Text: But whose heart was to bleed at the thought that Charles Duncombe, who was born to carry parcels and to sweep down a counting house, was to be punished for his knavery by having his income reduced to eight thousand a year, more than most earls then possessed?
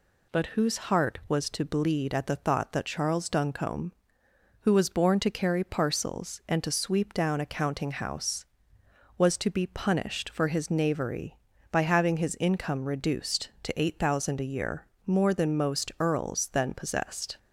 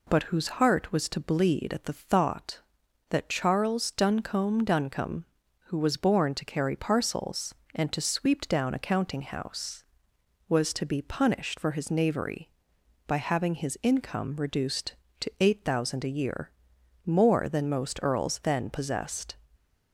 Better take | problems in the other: first | says "Duncombe" twice; at 4.6 s

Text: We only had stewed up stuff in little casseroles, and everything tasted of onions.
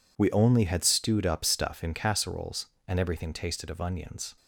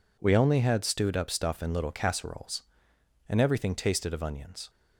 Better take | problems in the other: second | skips "little"; at 1.9 s

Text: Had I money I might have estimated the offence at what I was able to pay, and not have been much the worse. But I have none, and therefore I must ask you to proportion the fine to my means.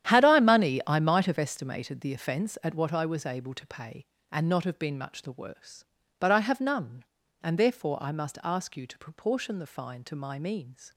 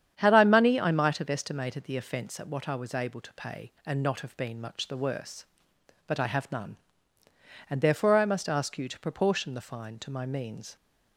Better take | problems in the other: second | gets quieter; strong; throughout; 14 dB // starts louder than the rest; strong; until 1.1 s; 10.5 dB; strong in the second

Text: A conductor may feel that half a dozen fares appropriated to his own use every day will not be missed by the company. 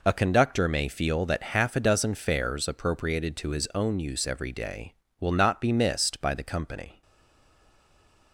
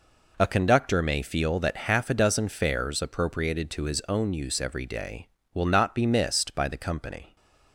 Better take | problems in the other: second | stays silent after the last word; noticeable; from 7.0 s on; 1.3 s long

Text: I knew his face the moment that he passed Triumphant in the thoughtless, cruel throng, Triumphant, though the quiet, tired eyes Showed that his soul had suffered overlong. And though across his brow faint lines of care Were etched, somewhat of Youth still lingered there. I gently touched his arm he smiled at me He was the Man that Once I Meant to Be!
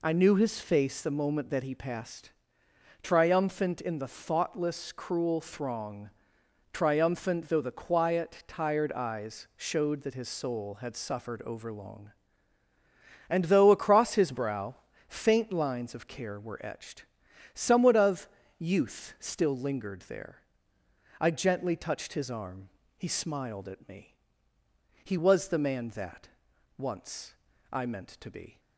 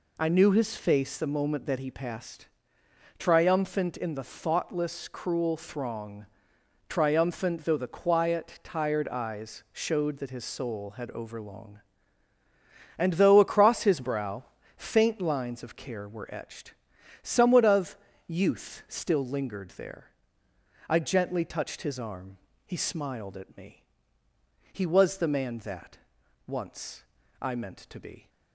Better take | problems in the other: first | pauses between "passed" and "Triumphant"; noticeable; at 2.4 s; 0.70 s long; noticeable in the first // skips "suffered"; at 11.1 s // pauses between "brow" and "faint"; slight; at 14.4 s; 0.32 s long; slight in the first // pauses between "of" and "Youth"; slight; at 17.9 s; 0.32 s long; slight in the first // pauses between "arm" and "he"; slight; at 22.3 s; 0.28 s long; slight in the first // pauses between "me" and "He"; noticeable; at 23.8 s; 0.88 s long; noticeable in the first // pauses between "that" and "Once"; noticeable; at 25.9 s; 0.50 s long; noticeable in the first // pauses between "Once" and "I"; at 27.0 s; 0.38 s long; also in the first

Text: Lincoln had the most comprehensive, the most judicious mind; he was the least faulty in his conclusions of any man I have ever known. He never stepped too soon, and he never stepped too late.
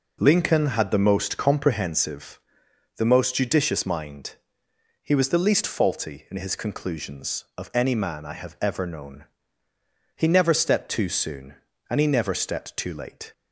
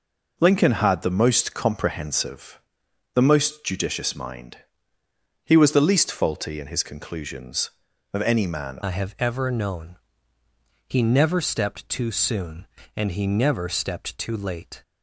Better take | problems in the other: first | changes voice at "I"; from 8.8 s on; 6.0 s long

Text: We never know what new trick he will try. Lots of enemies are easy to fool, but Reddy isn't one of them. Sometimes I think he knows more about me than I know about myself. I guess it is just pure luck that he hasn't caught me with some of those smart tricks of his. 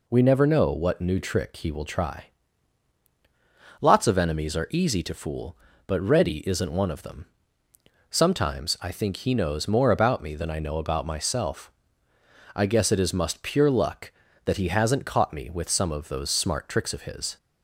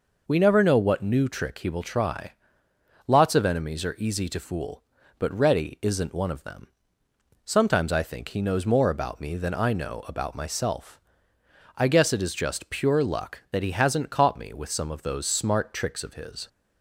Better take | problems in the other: second | says "must" for "just"; at 13.1 s

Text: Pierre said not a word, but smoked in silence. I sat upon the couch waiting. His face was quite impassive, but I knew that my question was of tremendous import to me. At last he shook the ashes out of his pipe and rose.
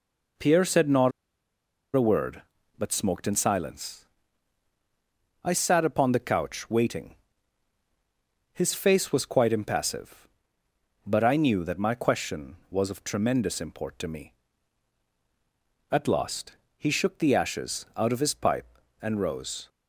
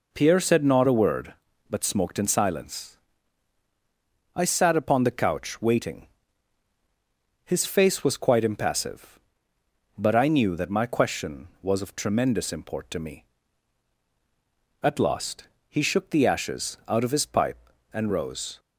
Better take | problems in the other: second | pauses between "not" and "a"; noticeable; at 1.1 s; 0.85 s long // pauses between "last" and "he"; slight; at 16.5 s; 0.20 s long; slight in the second

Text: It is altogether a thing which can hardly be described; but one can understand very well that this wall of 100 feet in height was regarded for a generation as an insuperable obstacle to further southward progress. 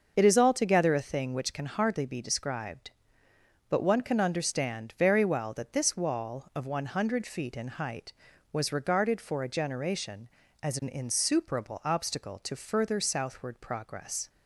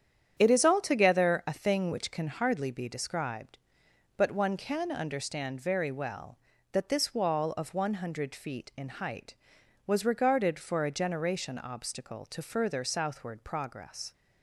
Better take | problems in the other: first | starts louder than the rest; strong; until 1.3 s; 9 dB; also in the first // skips "as an insuperable"; at 11.5 s

